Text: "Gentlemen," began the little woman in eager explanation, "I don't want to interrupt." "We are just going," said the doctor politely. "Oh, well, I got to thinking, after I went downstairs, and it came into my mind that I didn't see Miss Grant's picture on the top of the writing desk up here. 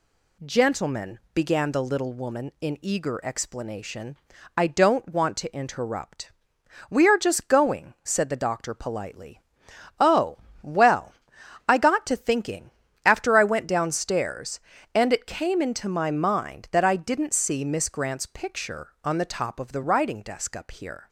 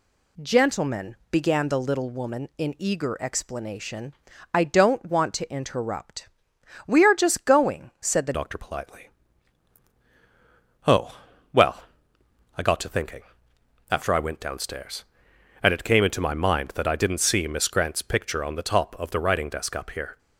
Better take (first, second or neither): first